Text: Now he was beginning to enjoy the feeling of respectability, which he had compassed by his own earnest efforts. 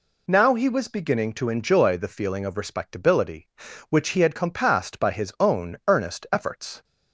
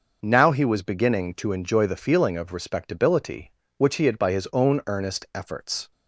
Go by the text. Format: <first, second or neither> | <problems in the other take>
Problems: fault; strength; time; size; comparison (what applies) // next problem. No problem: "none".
first | skips "compassed"; at 4.1 s